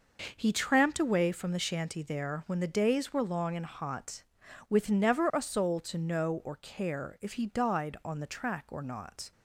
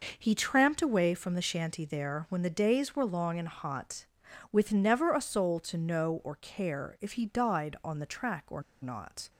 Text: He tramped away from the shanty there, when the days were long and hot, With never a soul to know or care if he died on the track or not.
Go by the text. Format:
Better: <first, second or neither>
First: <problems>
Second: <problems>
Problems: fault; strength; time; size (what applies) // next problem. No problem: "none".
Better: first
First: none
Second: pauses between "or" and "not"; slight; at 8.6 s; 0.21 s long